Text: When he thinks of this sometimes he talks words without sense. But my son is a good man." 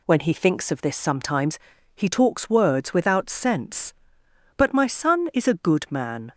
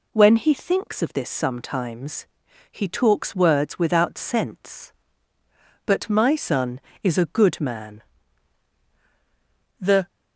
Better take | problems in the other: first | pauses between "sometimes" and "he"; at 2.2 s; 0.44 s long; slight in the first // goes on to say "The"; slight; from 9.7 s on; 0.28 s long

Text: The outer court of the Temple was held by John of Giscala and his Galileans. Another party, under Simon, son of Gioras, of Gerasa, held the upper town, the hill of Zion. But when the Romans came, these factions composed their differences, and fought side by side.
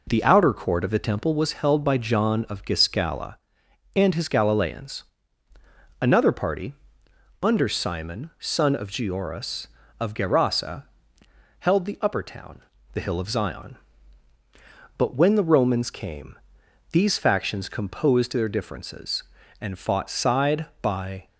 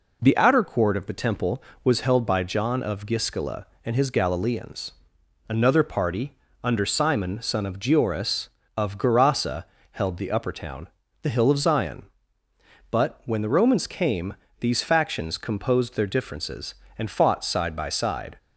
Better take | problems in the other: second | stops before "side"; at 21.2 s

